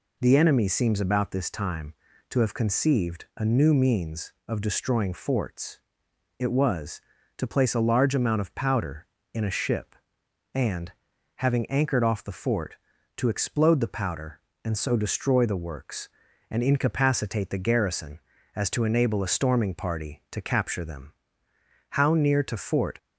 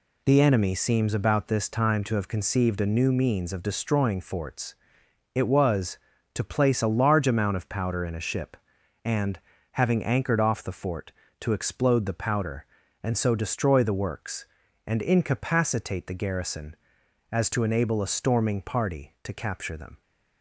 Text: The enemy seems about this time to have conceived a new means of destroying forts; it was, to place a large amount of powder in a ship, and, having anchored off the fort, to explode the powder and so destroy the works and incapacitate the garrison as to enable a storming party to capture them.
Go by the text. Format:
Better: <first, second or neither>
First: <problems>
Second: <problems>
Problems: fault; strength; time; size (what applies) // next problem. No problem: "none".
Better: second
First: goes on to say "How near to Fort"; noticeable; from 21.8 s on; 1.0 s long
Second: none